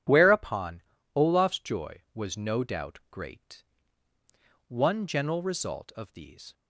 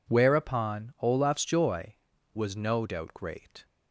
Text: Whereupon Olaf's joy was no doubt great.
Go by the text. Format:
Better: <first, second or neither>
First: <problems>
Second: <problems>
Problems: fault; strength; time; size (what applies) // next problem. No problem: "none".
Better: second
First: pauses between "Whereupon" and "Olaf's"; slight; at 0.7 s; 0.34 s long // goes on to say "One general result of these"; strong; from 4.6 s on; 1.8 s long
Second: none